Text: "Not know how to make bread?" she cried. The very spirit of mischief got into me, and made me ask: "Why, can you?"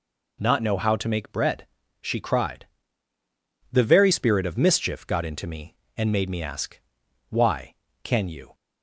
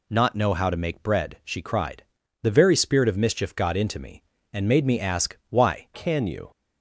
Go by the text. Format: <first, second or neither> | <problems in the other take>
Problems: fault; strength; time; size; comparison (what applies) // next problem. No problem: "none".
first | changes voice at "can"; from 5.9 s on; 0.5 s long